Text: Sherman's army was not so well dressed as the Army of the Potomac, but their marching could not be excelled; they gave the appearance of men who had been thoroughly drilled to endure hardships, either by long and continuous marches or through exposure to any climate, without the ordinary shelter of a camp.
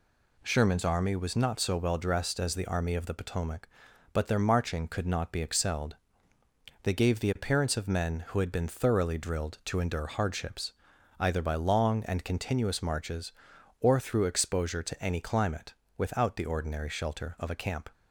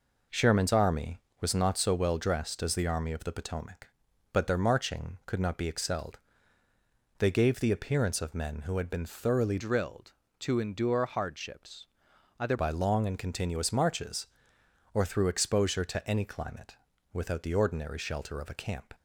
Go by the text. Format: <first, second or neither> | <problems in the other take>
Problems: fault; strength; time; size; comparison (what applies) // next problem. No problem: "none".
first | changes voice from "drilled" to "either"; from 9.5 to 12.5 s; 3.0 s long